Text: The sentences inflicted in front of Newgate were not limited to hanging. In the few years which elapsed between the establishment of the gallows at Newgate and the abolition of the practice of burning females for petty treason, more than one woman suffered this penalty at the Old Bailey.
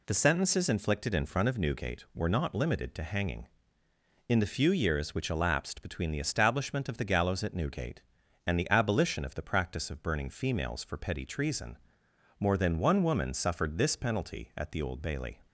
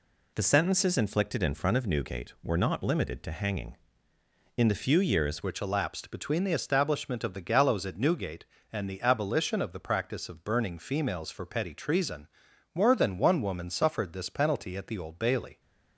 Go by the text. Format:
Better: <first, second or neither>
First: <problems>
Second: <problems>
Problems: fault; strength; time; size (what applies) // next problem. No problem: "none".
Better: first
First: none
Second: changes voice at "which"; from 5.4 s on; 10.1 s long